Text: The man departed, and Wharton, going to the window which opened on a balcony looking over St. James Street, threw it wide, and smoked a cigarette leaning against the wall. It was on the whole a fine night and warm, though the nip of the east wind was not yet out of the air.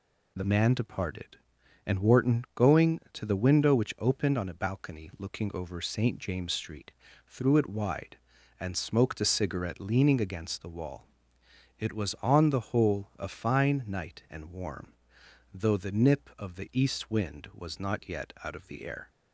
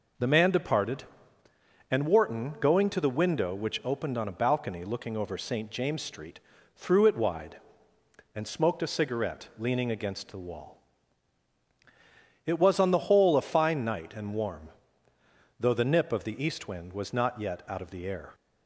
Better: second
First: changes voice at "man"; from 0.4 s on; 18.6 s long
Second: none

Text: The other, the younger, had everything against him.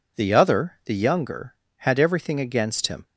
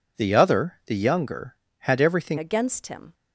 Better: first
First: none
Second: changes voice at "against"; from 2.3 s on; 0.8 s long

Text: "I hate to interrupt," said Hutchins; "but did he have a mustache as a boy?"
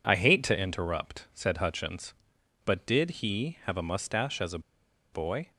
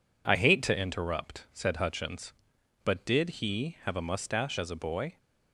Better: second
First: pauses between "a" and "boy"; noticeable; at 4.5 s; 0.53 s long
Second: none

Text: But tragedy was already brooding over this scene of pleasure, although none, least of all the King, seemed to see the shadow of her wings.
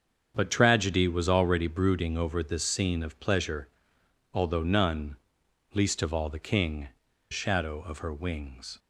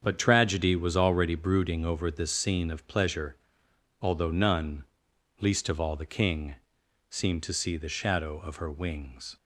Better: second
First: starts louder than the rest; strong; until 1.3 s; 7 dB // skips "seemed to see the"; at 7.1 s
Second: starts louder than the rest; strong; until 1.0 s; 7.5 dB

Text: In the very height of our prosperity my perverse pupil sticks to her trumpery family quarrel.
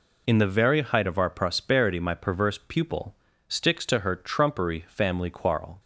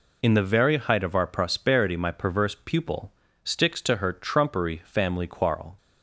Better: neither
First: pauses between "pupil" and "sticks"; slight; at 3.1 s; 0.34 s long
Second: pauses between "pupil" and "sticks"; slight; at 3.1 s; 0.32 s long

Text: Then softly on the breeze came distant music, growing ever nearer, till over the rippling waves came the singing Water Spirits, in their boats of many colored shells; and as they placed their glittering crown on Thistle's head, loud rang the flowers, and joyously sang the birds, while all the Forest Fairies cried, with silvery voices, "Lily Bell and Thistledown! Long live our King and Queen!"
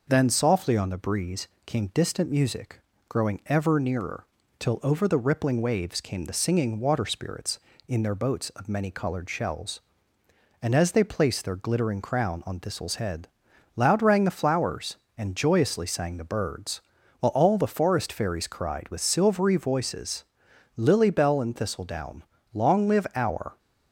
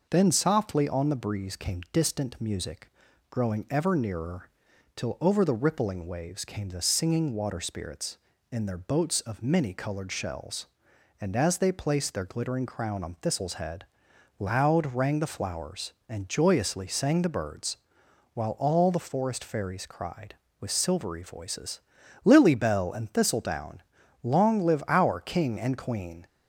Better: second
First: pauses between "breeze" and "came"; slight; at 1.4 s; 0.18 s long // stops before "King and Queen"; at 23.5 s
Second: none

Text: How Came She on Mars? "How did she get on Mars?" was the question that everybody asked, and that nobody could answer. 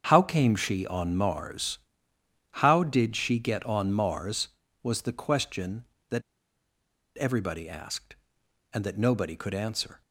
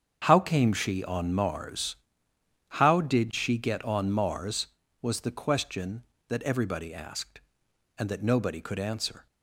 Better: second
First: starts louder than the rest; strong; until 1.1 s; 7.5 dB // pauses between "that" and "everybody"; noticeable; at 6.2 s; 0.97 s long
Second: starts louder than the rest; strong; until 1.2 s; 7.5 dB

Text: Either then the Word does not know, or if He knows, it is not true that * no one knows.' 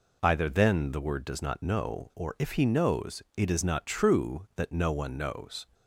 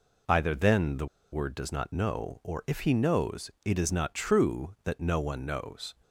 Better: first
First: none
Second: pauses between "the" and "Word"; slight; at 1.0 s; 0.27 s long

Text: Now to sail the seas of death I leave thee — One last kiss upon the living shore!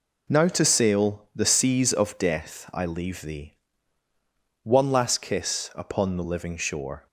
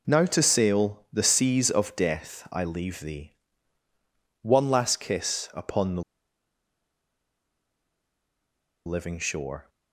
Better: first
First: none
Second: pauses between "the" and "living"; strong; at 6.0 s; 2.8 s long

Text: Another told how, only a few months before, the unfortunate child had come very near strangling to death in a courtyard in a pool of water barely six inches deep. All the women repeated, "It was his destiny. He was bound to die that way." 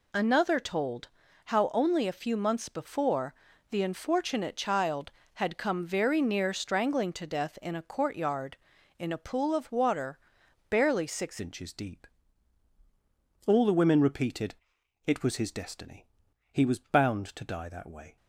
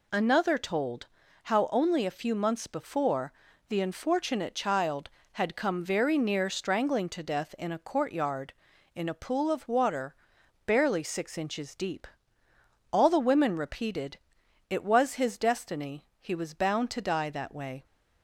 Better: second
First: pauses between "told" and "how"; at 1.0 s; 0.38 s long // pauses between "water" and "barely"; noticeable; at 10.1 s; 0.50 s long // changes voice at "inches"; from 11.3 s on; 6.8 s long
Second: pauses between "told" and "how"; at 1.0 s; 0.38 s long // pauses between "water" and "barely"; noticeable; at 10.1 s; 0.50 s long

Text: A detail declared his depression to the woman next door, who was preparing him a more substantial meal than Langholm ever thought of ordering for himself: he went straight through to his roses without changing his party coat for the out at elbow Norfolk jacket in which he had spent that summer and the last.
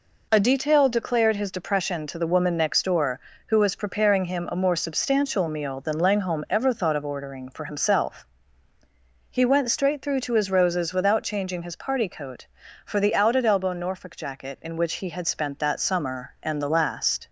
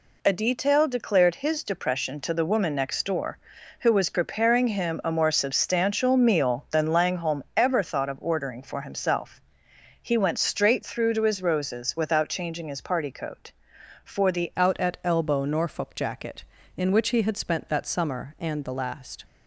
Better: first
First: none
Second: changes voice at "out"; from 14.5 s on; 4.7 s long

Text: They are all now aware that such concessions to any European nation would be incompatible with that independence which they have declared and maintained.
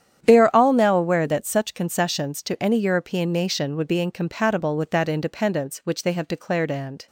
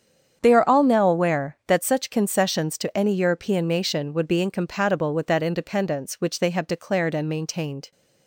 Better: second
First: starts louder than the rest; strong; until 1.2 s; 9.5 dB // stops before "maintained"; at 7.0 s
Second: starts louder than the rest; strong; until 1.4 s; 8 dB

